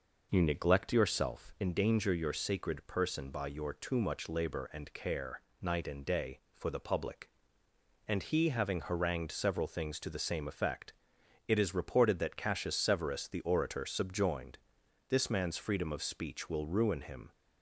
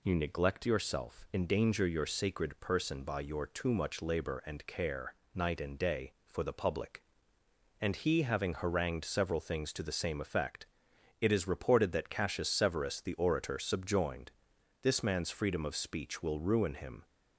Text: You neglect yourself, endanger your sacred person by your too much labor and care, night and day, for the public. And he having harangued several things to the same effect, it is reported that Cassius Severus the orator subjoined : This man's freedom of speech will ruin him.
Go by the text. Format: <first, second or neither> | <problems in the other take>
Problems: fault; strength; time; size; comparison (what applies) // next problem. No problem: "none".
second | starts louder than the rest; noticeable; until 1.6 s; 5.5 dB